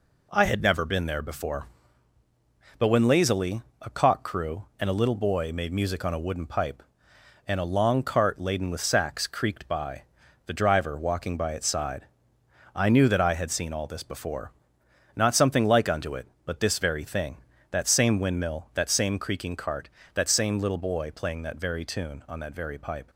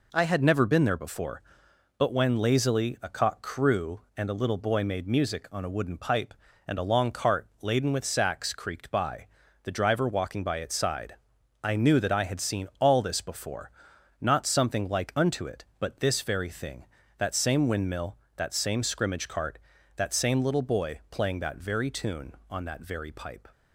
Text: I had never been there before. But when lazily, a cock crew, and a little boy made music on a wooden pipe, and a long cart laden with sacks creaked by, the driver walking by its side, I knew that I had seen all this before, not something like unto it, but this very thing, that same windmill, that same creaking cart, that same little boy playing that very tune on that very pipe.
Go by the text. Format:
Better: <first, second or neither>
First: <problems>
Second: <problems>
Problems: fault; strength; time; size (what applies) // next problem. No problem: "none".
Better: first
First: none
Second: pauses between "cart" and "laden"; slight; at 7.4 s; 0.16 s long // says "scrimmage" for "creaking"; at 18.8 s